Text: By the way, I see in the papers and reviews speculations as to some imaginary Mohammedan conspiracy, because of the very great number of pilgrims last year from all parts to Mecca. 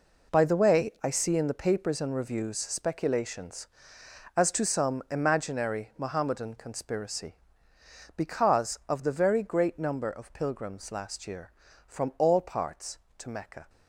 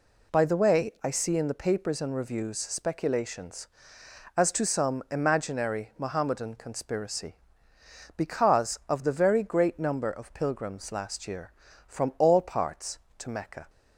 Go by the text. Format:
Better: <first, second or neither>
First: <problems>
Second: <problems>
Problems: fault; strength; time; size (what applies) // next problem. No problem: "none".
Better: second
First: gets quieter; strong; throughout; 10.5 dB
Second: none